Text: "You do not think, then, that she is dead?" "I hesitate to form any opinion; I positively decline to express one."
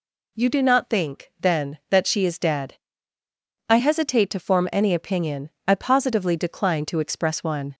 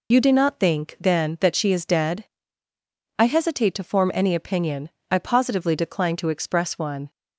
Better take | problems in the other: first | loses the start of "You"; at 0.1 s; 55 ms

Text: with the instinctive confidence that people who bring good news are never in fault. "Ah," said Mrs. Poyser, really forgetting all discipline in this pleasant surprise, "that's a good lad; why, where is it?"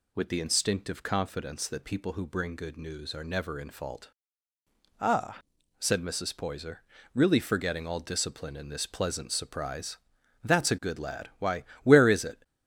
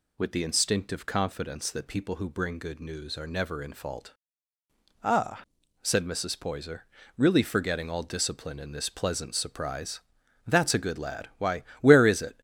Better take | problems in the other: neither | none

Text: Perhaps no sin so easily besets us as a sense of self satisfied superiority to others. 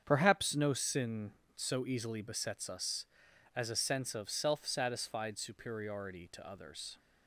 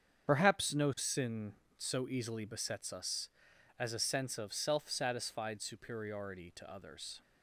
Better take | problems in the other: first | loses the start of "Perhaps"; at 0.2 s; 45 ms // starts louder than the rest; strong; until 1.3 s; 8 dB; strong in the first

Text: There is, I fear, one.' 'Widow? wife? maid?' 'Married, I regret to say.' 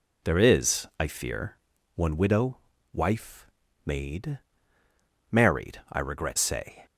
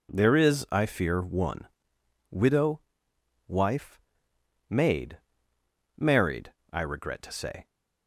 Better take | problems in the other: second | skips "to"; at 6.3 s

